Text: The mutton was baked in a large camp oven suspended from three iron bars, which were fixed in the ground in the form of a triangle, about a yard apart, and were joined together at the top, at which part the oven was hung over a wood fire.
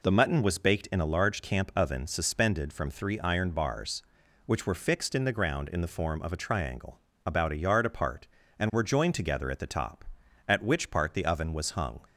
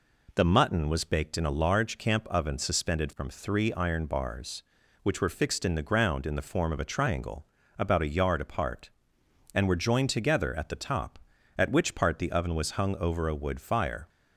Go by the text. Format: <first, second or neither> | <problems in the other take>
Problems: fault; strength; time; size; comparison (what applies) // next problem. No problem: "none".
second | stops before "over a wood fire"; at 12.0 s